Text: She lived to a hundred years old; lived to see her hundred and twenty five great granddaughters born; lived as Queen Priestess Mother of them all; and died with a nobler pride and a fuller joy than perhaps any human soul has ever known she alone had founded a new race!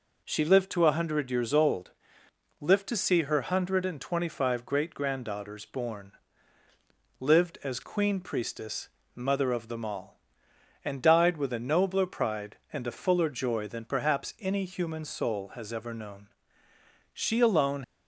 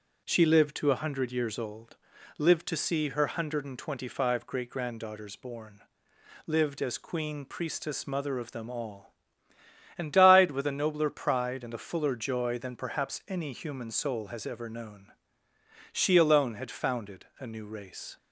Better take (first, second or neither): second